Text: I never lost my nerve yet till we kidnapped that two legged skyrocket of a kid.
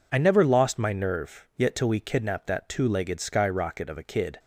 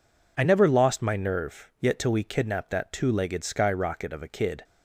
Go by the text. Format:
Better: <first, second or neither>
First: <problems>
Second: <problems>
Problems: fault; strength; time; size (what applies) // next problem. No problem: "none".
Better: neither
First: none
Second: none